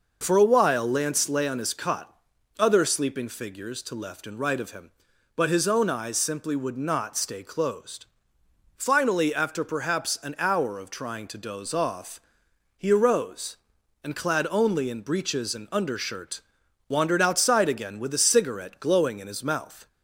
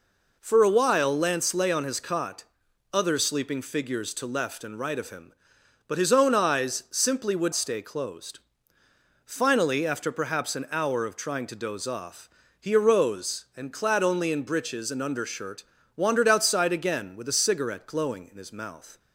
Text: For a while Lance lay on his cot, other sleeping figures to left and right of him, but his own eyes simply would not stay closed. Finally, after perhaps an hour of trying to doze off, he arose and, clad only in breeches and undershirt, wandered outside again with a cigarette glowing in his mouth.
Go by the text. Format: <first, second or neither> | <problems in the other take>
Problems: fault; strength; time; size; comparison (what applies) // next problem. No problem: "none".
first | skips "not"; at 7.5 s